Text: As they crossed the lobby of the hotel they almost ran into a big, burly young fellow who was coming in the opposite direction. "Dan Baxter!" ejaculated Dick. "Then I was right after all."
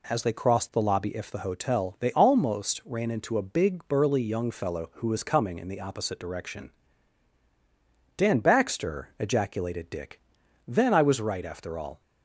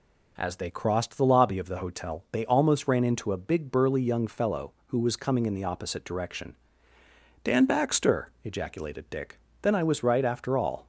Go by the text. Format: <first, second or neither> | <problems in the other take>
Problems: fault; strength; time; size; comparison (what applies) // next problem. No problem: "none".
second | says "if" for "of"; at 1.0 s